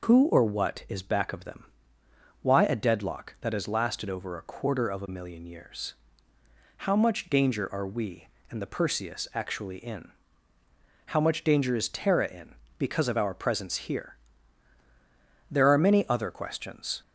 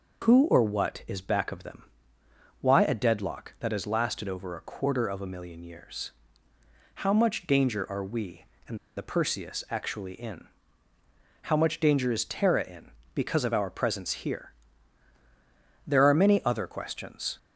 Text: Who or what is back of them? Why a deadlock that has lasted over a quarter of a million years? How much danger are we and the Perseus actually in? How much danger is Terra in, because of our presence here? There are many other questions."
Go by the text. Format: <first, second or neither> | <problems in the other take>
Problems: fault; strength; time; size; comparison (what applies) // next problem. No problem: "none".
first | pauses between "and" and "the"; slight; at 8.7 s; 0.19 s long